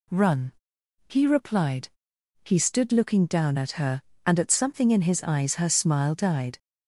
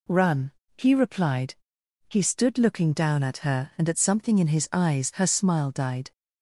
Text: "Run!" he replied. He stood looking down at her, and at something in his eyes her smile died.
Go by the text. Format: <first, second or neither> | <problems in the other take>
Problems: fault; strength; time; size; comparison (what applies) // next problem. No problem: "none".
neither | none